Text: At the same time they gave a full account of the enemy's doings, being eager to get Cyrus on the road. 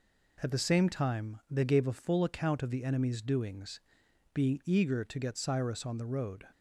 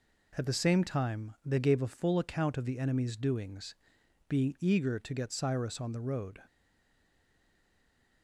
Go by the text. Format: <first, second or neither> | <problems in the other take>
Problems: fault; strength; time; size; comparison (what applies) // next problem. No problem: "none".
first | stays silent after the last word; noticeable; from 6.4 s on; 1.8 s long